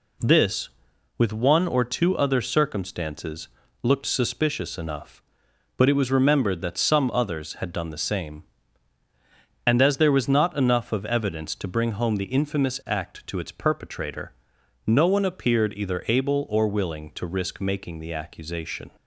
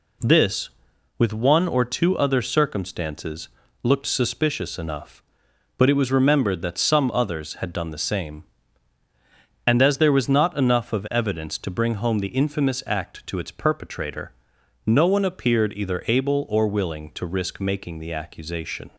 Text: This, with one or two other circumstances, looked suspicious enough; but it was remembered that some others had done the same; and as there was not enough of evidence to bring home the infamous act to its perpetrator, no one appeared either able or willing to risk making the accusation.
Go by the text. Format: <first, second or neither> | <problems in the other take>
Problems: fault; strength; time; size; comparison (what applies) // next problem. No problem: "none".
neither | none